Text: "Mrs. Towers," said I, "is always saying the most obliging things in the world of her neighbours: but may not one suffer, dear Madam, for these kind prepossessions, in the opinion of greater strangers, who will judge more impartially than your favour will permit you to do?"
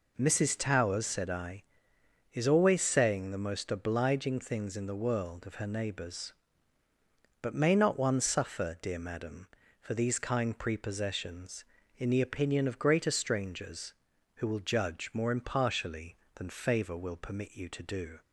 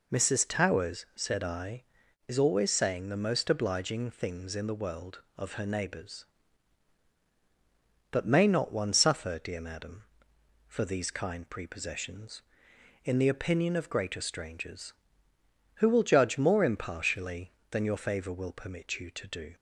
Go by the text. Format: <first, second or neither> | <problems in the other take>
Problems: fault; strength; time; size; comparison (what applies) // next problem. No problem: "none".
second | skips "your"; at 16.5 s